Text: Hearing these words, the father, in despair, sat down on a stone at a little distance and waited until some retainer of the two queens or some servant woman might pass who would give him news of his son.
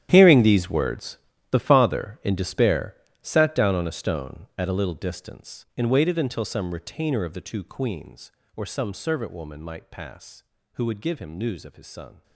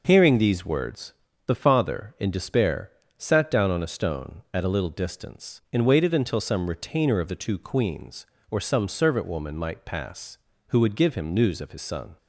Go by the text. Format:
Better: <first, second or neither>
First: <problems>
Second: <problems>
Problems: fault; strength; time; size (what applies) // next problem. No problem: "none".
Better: second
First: gets quieter; strong; throughout; 16 dB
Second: none